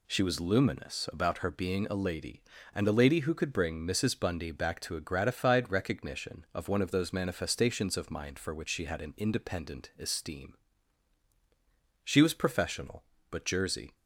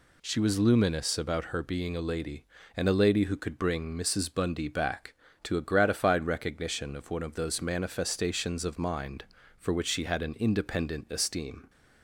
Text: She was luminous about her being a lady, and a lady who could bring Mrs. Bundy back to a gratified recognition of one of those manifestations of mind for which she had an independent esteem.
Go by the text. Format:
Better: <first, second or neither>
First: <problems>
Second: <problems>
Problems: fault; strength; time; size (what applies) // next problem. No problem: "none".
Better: second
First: goes on to say "She was professional but Jersey"; strong; from 12.0 s on; 1.9 s long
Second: none